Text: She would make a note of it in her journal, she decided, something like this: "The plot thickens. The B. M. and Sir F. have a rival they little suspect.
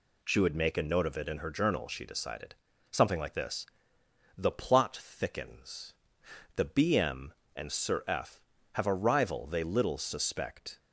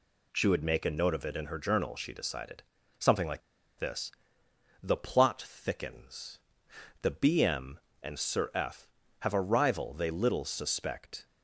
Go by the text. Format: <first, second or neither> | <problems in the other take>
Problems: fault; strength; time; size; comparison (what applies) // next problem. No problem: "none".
first | pauses between "like" and "this"; at 3.4 s; 0.38 s long